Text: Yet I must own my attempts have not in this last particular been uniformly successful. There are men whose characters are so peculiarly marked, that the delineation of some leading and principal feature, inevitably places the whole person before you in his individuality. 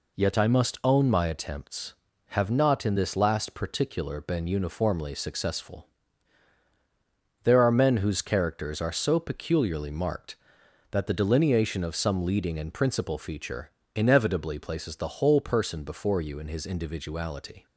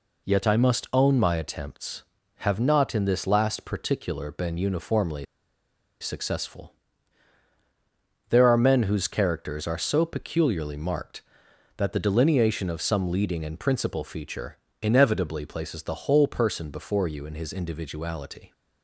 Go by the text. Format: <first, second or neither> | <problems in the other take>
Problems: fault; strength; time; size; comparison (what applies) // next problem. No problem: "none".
first | pauses between "uniformly" and "successful"; noticeable; at 5.2 s; 0.76 s long